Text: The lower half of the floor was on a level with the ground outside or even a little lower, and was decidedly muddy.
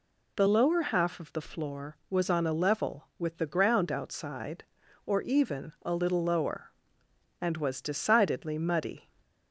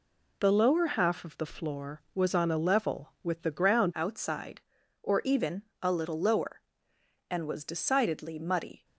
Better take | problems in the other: first | changes voice at "outside"; from 3.9 s on; 4.9 s long // pauses between "even" and "a"; slight; at 5.6 s; 0.18 s long

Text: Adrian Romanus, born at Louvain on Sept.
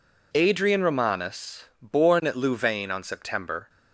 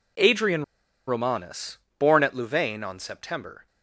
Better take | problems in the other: first | pauses between "Adrian" and "Romanus"; at 0.6 s; 0.44 s long

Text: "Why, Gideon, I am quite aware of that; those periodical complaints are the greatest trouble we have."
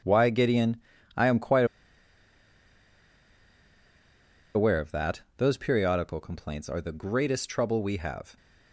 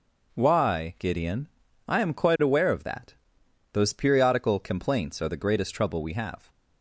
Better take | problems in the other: second | pauses between "quite" and "aware"; strong; at 1.6 s; 2.9 s long

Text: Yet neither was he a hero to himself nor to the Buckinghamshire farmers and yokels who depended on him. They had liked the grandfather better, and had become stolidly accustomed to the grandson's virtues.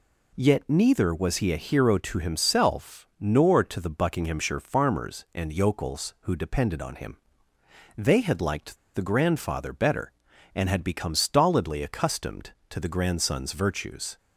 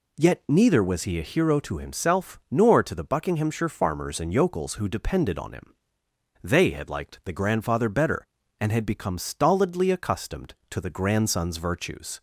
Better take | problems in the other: second | pauses between "liked" and "the"; slight; at 8.7 s; 0.18 s long

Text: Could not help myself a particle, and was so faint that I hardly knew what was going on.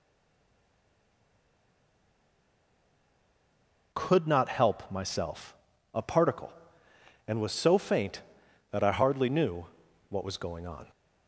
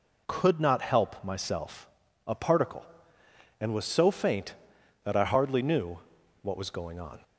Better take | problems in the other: second | stays silent before the first word; strong; until 3.9 s; 3.9 s long // pauses between "myself" and "a"; at 5.5 s; 0.38 s long; also in the second // pauses between "knew" and "what"; at 9.6 s; 0.44 s long; also in the second

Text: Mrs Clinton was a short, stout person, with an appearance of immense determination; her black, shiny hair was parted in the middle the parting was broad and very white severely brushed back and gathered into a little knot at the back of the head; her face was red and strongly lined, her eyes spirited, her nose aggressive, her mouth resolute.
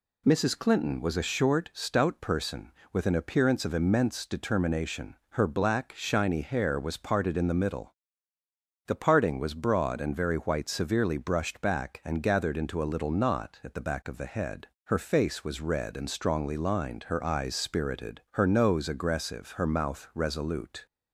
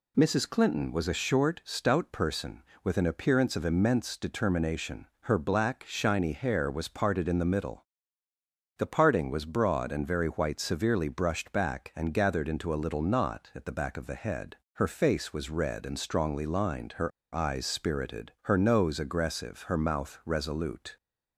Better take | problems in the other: first | pauses between "middle" and "the"; noticeable; at 7.8 s; 0.94 s long; noticeable in the first // pauses between "her" and "eyes"; slight; at 17.1 s; 0.23 s long

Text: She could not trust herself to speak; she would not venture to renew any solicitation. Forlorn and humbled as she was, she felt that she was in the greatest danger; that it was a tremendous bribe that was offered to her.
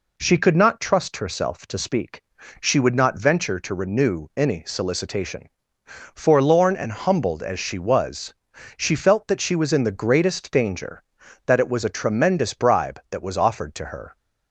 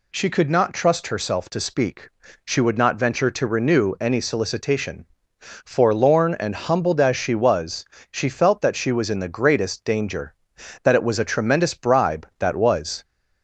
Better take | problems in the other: first | stops before "offered to her"; at 13.0 s

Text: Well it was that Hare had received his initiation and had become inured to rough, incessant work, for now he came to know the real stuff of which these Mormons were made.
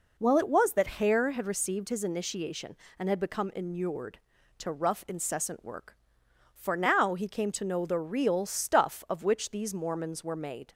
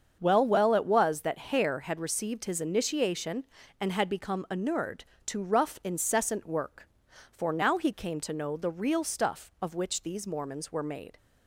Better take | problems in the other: first | starts louder than the rest; until 1.2 s; 7 dB // says "Well" twice; at 0.4 s

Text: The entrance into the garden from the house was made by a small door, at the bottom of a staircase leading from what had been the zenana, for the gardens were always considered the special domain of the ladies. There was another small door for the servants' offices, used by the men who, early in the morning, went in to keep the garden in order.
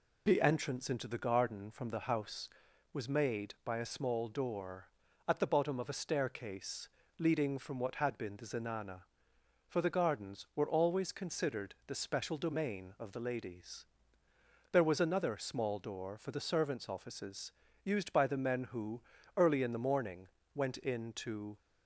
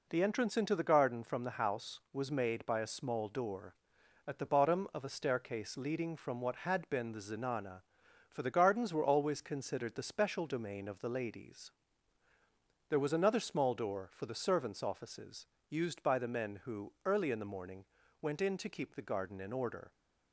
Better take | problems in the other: second | pauses between "staircase" and "leading"; slight; at 6.8 s; 0.28 s long // stops before "keep the garden in order"; at 21.5 s

